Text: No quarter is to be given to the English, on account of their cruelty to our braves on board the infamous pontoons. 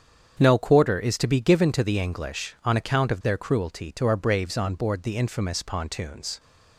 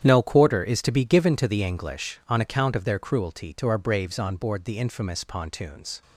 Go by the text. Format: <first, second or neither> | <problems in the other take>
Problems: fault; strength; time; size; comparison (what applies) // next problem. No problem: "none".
first | gets quieter; strong; throughout; 13.5 dB // starts louder than the rest; strong; until 1.0 s; 9.5 dB; strong in the first